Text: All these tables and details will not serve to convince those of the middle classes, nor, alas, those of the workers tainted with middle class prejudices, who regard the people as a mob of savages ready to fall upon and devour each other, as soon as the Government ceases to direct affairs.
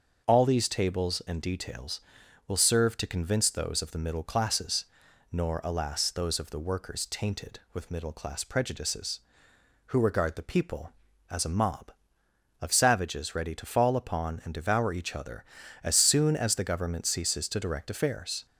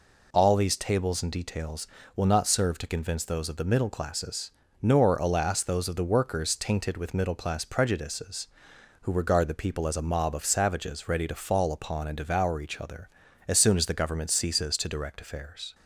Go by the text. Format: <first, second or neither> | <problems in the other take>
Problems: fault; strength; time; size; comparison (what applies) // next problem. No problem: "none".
second | starts louder than the rest; until 1.3 s; 6.5 dB // skips "not"; at 2.5 s